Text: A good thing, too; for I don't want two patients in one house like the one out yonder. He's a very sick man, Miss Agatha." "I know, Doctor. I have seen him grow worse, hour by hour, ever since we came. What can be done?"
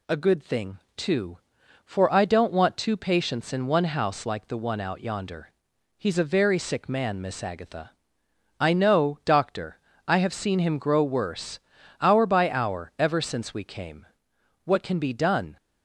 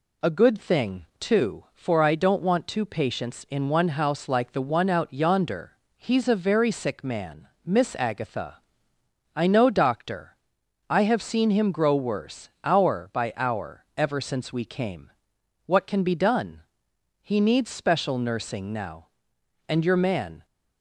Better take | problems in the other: first | goes on to say "He needs special nursing now and your man"; strong; from 17.2 s on; 3.2 s long

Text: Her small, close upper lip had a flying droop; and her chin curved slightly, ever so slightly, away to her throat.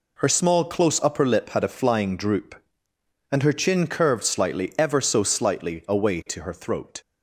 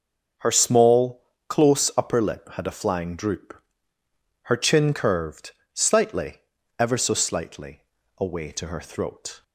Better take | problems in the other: first | starts louder than the rest; noticeable; until 1.6 s; 6 dB // skips "and"; at 3.9 s // pauses between "curved" and "slightly"; slight; at 5.5 s; 0.22 s long

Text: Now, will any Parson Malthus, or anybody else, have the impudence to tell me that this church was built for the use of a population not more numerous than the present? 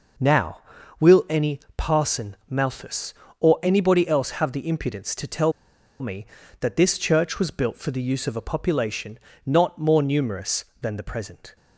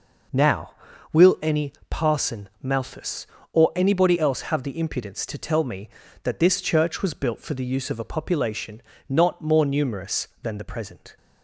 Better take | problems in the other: second | pauses between "any" and "Parson"; slight; at 1.5 s; 0.18 s long; slight in the second // pauses between "tell" and "me"; noticeable; at 5.5 s; 0.49 s long // pauses between "population" and "not"; slight; at 9.1 s; 0.26 s long; slight in the second

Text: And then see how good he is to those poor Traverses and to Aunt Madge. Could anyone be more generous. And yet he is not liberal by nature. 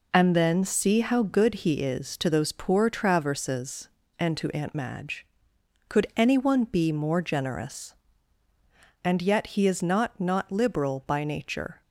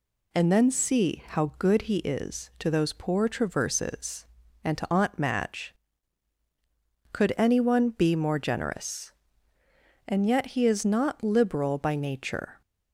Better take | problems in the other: second | says "not" twice; at 10.1 s

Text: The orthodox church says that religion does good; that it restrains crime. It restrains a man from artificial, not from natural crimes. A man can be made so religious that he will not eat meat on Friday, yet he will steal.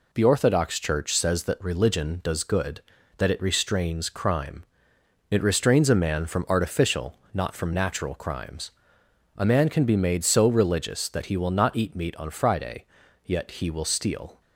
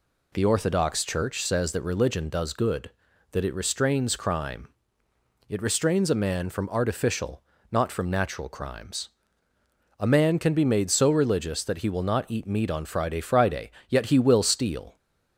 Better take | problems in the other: first | says "Friday" twice; at 13.1 s

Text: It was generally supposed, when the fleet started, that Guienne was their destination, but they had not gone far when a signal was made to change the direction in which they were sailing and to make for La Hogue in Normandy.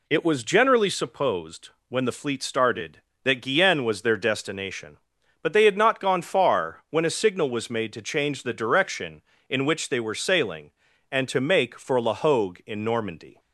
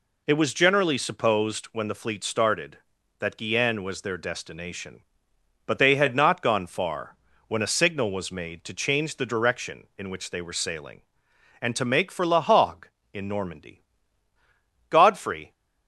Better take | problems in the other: first | pauses between "far" and "when"; slight; at 7.1 s; 0.32 s long // goes on to say "Godfrey"; noticeable; from 14.8 s on; 0.62 s long

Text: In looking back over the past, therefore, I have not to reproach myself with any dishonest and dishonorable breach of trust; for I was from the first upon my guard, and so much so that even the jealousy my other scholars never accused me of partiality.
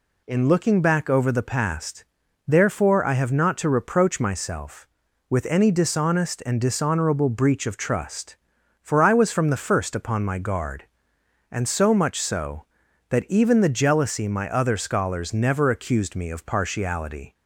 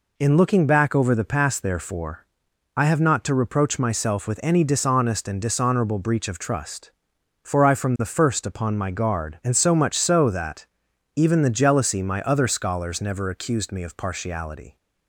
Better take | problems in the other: first | skips "was"; at 7.7 s // pauses between "that" and "even"; noticeable; at 10.6 s; 0.48 s long

